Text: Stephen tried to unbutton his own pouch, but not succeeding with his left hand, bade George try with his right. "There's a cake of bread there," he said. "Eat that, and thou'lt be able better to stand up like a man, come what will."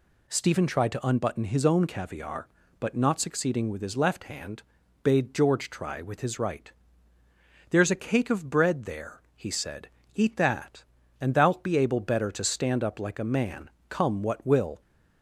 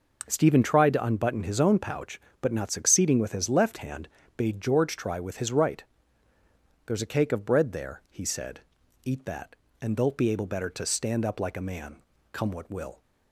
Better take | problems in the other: second | says "caviar" for "pouch"; at 1.8 s

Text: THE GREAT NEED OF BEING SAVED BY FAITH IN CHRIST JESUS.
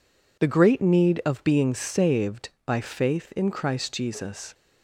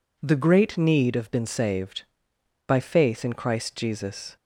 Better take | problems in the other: first | says "Been" for "BEING"; at 1.2 s

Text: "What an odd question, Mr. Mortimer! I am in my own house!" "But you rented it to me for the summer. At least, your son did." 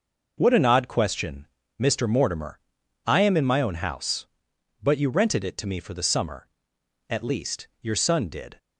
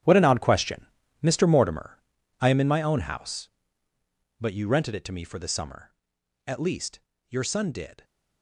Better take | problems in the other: first | gets quieter; strong; throughout; 13.5 dB

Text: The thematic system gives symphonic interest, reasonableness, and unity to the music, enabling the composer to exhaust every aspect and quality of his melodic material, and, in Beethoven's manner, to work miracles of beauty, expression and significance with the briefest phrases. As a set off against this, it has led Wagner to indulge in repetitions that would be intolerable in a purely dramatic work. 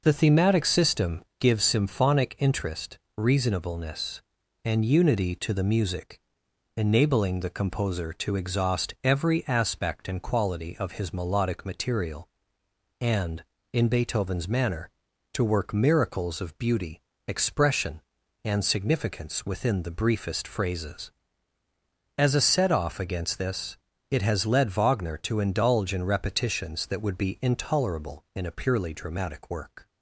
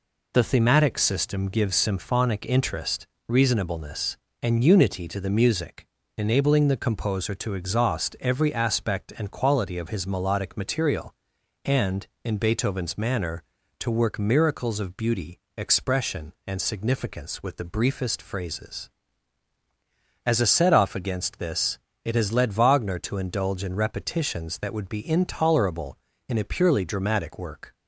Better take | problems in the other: second | pauses between "system" and "gives"; slight; at 1.2 s; 0.16 s long // says "within" for "with"; at 19.4 s

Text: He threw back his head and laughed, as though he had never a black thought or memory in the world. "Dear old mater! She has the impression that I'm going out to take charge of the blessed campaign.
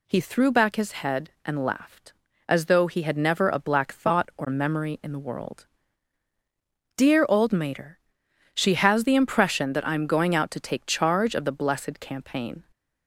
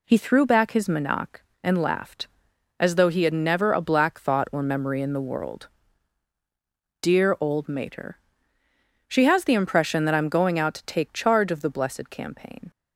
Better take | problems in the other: first | says "manak" for "head"; at 0.8 s

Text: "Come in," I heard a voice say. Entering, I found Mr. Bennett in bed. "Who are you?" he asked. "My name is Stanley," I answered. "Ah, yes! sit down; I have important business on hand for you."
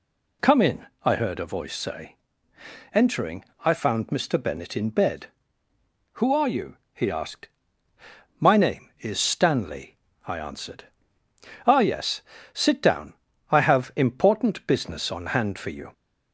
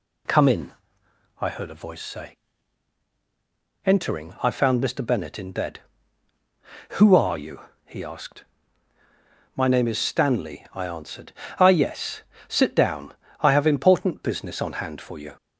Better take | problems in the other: neither | none

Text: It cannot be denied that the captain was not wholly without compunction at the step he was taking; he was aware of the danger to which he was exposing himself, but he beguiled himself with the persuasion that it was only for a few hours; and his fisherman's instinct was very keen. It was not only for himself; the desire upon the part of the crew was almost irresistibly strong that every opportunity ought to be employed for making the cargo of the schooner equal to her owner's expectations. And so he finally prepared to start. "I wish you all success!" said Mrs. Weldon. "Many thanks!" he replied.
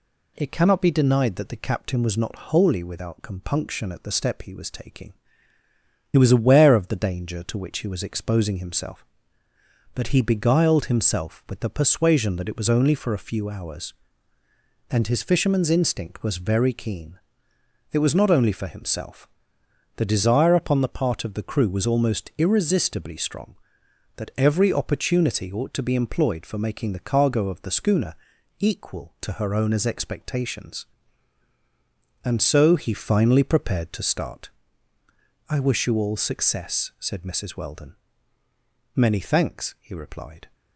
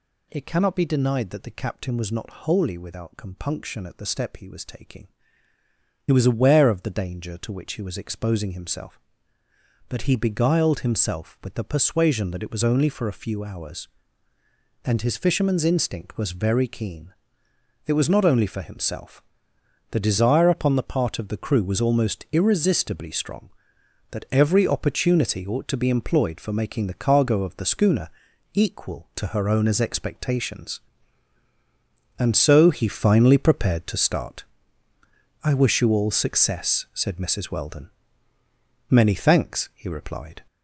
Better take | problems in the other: first | gets louder; noticeable; throughout; 5.5 dB // pauses between "schooner" and "equal"; noticeable; at 28.0 s; 0.46 s long; noticeable in the first

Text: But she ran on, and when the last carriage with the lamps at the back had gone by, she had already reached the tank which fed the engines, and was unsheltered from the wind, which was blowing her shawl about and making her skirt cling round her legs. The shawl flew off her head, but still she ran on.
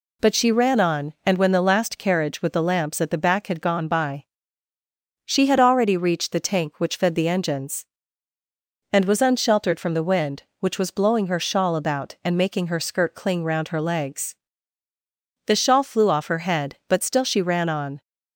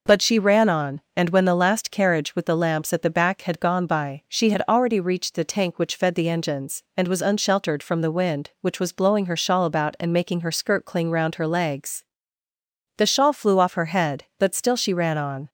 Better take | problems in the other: neither | none

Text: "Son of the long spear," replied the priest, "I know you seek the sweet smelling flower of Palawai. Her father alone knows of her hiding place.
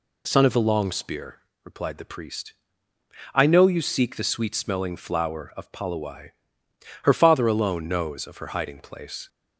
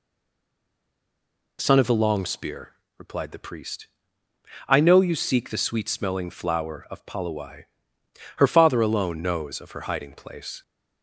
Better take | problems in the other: first | stays silent before the first word; noticeable; until 1.5 s; 1.5 s long

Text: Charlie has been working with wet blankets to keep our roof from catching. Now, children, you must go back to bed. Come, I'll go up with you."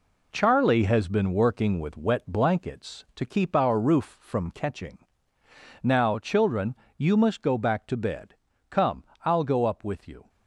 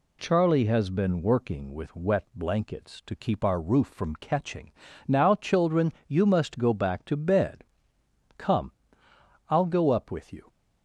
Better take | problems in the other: second | gets quieter; strong; throughout; 8 dB

